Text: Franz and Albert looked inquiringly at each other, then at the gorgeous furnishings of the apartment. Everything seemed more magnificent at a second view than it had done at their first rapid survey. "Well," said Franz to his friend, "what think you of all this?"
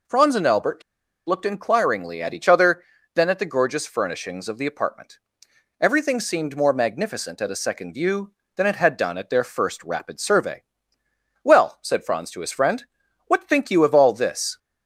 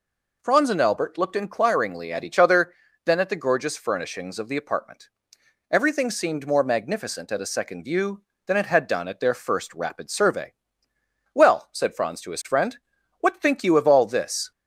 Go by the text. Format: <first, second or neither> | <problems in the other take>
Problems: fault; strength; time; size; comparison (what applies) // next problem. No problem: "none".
second | pauses between "Albert" and "looked"; at 0.8 s; 0.45 s long